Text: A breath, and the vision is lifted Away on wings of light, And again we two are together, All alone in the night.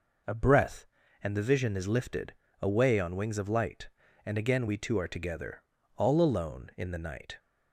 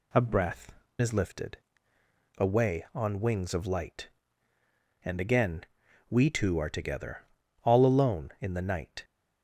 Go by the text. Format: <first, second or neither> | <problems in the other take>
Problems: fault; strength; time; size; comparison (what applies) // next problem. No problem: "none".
first | skips "and the vision"; at 0.8 s // pauses between "lifted" and "Away"; noticeable; at 1.5 s; 0.80 s long; slight in the first // pauses between "again" and "we"; noticeable; at 5.6 s; 0.46 s long